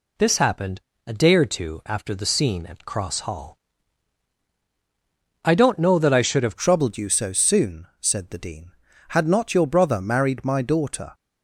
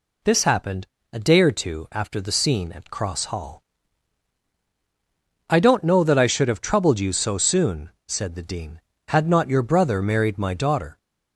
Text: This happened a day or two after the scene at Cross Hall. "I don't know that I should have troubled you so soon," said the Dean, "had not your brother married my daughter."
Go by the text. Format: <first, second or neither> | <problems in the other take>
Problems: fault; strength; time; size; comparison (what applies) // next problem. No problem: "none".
second | pauses between "happened" and "a"; slight; at 0.8 s; 0.28 s long; slight in the second // changes voice at "troubled"; from 6.5 s on; 4.6 s long